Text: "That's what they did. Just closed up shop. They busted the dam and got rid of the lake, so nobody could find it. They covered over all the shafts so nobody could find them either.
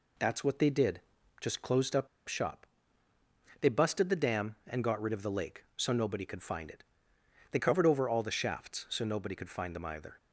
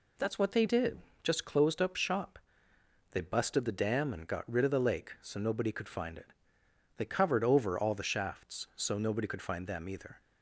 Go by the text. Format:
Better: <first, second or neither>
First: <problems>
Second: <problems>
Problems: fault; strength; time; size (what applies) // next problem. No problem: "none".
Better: second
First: pauses between "up" and "shop"; slight; at 2.0 s; 0.19 s long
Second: none